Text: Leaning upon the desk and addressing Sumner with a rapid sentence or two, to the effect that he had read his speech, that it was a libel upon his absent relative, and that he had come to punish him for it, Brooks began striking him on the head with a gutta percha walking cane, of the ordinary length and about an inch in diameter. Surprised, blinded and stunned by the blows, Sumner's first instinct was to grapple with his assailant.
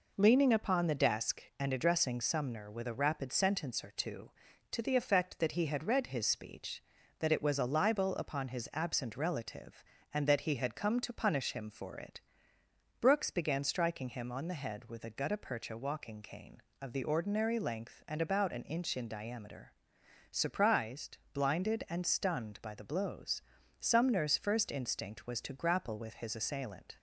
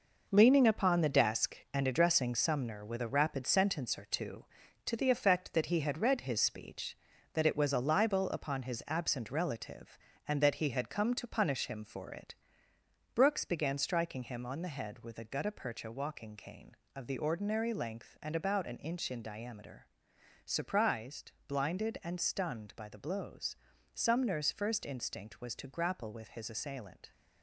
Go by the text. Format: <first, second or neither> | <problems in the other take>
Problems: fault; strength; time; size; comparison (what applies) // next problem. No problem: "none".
first | gets quieter; strong; throughout; 8.5 dB